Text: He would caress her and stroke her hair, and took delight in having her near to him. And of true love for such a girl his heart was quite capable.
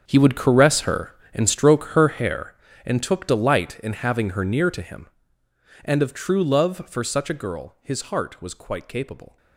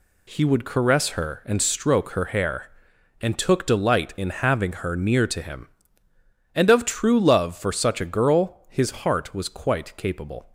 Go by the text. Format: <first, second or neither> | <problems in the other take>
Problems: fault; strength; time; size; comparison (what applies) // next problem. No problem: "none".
second | gets quieter; strong; throughout; 16 dB